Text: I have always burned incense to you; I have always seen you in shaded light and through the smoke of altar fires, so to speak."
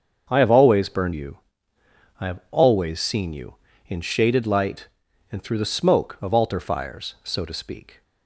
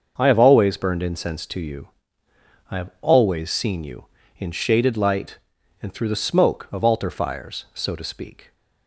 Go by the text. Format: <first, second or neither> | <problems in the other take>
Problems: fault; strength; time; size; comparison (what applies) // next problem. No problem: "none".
second | starts louder than the rest; until 1.3 s; 6.5 dB; also in the second // skips "incense to"; at 1.1 s